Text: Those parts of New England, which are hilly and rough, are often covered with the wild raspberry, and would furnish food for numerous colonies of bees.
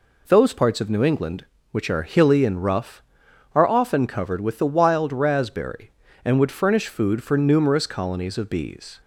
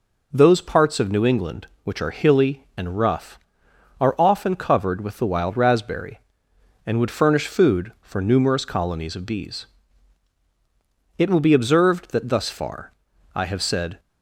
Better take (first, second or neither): first